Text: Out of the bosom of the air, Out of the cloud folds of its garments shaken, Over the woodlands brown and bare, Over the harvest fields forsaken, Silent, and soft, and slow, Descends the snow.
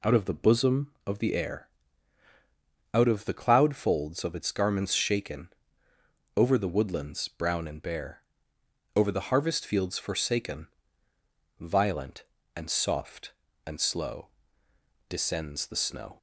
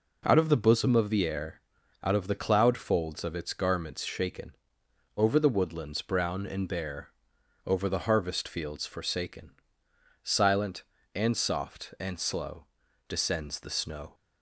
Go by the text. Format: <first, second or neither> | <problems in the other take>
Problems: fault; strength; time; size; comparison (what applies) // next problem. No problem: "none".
second | says "Violent" for "Silent"; at 11.5 s